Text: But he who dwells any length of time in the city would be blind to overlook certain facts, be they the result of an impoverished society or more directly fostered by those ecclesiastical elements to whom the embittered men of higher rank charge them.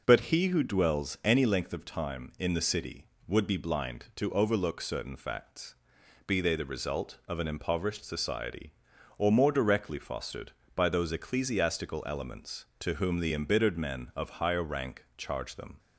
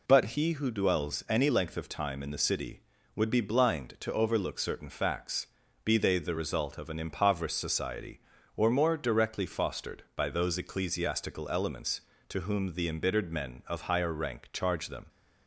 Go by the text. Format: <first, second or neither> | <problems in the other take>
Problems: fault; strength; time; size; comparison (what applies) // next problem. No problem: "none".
neither | none